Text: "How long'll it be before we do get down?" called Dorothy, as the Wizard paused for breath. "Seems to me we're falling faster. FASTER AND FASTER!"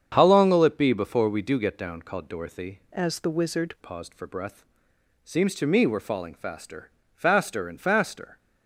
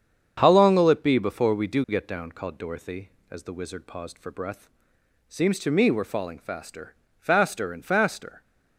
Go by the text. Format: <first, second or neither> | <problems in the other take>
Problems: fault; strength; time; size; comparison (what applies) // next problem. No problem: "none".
second | starts louder than the rest; strong; until 1.1 s; 7.5 dB; strong in the second // changes voice from "as" to "Wizard"; from 2.9 to 3.7 s; 0.8 s long